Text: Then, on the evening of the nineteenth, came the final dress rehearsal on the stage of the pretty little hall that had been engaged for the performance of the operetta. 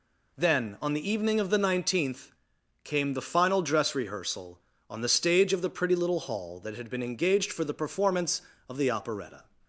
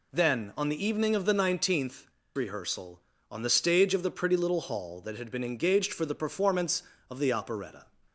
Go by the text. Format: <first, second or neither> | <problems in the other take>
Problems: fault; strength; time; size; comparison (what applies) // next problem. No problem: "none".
first | skips "came the final dress"; at 2.2 s